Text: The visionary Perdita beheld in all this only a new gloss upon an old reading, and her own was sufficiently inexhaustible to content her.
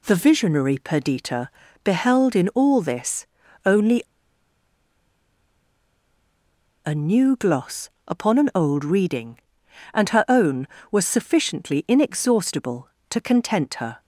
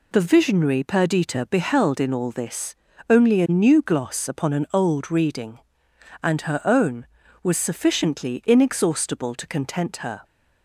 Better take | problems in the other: second | pauses between "Perdita" and "beheld"; slight; at 1.4 s; 0.36 s long // pauses between "this" and "only"; at 3.2 s; 0.40 s long; slight in the second // pauses between "only" and "a"; strong; at 4.0 s; 2.8 s long // pauses between "gloss" and "upon"; slight; at 7.8 s; 0.18 s long

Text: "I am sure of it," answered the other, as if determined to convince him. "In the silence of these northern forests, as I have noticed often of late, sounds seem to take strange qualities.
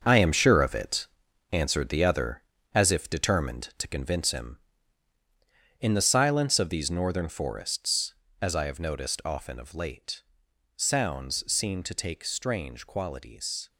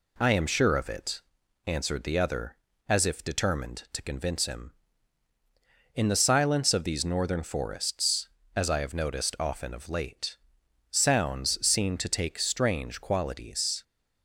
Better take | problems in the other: second | gets quieter; strong; throughout; 9.5 dB

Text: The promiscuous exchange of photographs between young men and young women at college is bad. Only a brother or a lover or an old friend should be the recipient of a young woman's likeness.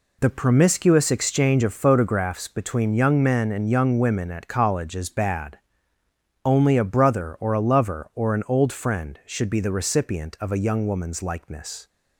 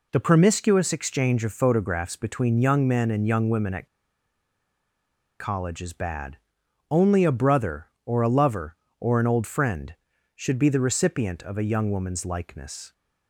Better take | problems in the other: first | pauses between "at" and "college"; strong; at 3.8 s; 1.5 s long

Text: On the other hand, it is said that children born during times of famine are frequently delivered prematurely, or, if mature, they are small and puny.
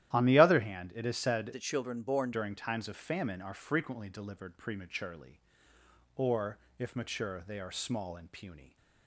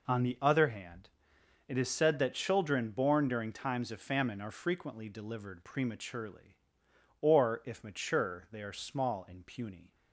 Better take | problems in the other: second | starts louder than the rest; strong; until 1.1 s; 12.5 dB // changes voice from "that" to "born"; from 1.5 to 2.3 s; 0.8 s long

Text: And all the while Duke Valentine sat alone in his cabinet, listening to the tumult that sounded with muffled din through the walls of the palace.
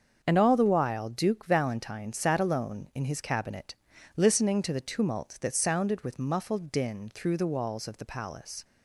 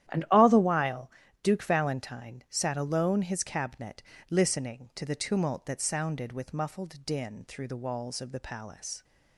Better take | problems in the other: first | starts louder than the rest; strong; until 1.4 s; 11.5 dB; also in the first // pauses between "while" and "Duke"; slight; at 1.0 s; 0.32 s long // skips "in"; at 3.2 s

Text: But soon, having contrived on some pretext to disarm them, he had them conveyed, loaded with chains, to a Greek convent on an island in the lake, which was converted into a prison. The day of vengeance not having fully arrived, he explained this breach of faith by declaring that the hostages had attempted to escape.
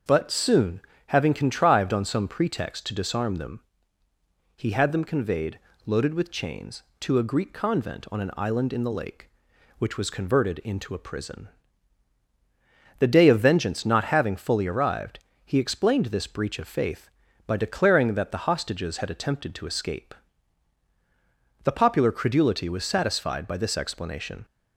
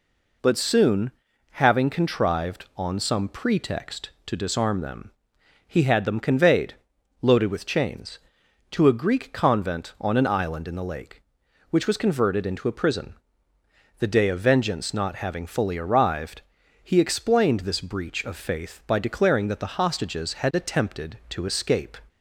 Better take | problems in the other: second | starts louder than the rest; until 1.3 s; 7 dB // goes on to say "The popular credulity was satisfied by this explanation"; strong; from 21.6 s on; 2.8 s long

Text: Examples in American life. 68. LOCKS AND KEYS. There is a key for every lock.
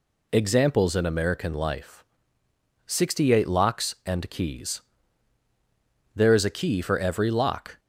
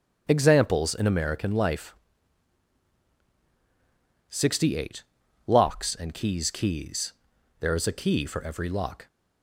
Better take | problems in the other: first | starts louder than the rest; strong; until 1.2 s; 8 dB // says "KEYS" twice; at 6.5 s

